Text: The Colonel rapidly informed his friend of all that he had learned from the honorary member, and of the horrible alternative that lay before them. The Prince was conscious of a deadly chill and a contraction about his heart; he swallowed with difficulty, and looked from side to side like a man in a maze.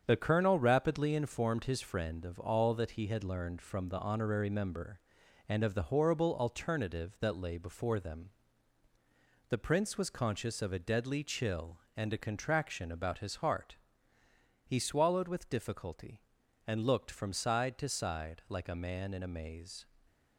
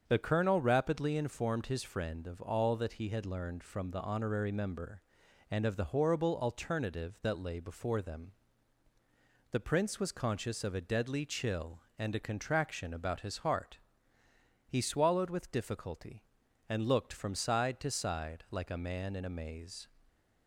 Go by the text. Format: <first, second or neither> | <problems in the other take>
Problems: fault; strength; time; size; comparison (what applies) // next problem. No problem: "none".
second | gets quieter; noticeable; throughout; 5.5 dB // starts louder than the rest; strong; until 1.0 s; 7.5 dB; also in the second